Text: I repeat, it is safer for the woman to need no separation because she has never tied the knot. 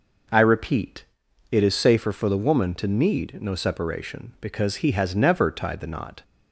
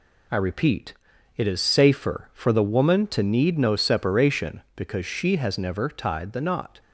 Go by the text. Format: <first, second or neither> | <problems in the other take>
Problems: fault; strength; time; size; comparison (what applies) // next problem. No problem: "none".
second | says "he" for "she"; at 4.7 s